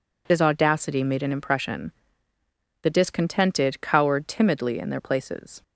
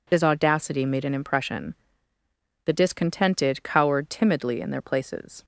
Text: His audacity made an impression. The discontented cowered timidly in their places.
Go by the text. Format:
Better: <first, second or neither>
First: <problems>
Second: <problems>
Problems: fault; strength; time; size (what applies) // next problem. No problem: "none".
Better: neither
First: none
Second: none